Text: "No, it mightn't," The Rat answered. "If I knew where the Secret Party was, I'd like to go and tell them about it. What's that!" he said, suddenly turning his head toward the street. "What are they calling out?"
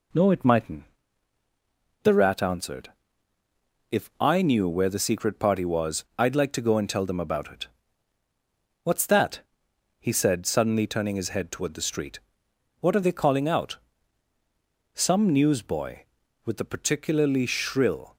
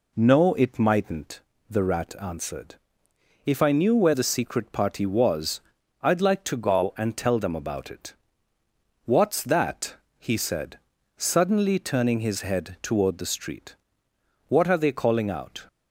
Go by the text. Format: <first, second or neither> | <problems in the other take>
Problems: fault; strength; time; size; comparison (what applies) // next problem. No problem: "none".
second | goes on to say "Some newsboy with a particularly shrill"; strong; from 14.9 s on; 3.2 s long